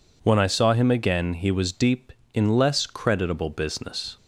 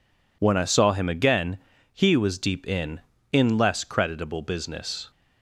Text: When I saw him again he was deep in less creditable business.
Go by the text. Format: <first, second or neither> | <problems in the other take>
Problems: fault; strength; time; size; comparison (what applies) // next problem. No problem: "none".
first | pauses between "again" and "he"; slight; at 1.5 s; 0.34 s long // says "in" twice; at 3.3 s